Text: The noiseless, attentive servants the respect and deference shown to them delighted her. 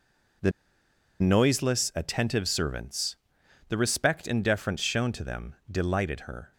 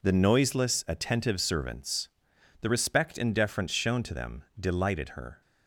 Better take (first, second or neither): second